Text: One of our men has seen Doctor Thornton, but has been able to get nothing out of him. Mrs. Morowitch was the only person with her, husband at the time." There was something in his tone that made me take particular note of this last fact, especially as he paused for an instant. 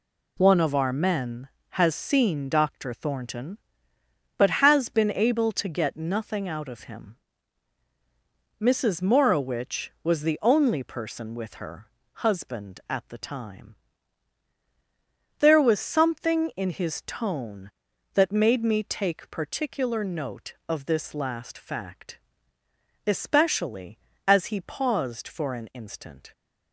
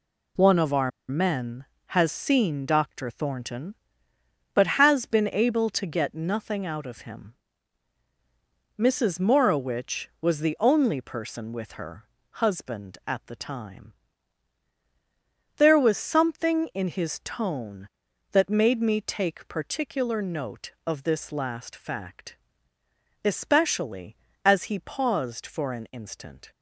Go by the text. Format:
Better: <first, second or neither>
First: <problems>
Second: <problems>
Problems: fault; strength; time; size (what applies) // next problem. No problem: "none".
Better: first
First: none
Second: pauses between "our" and "men"; slight; at 0.9 s; 0.18 s long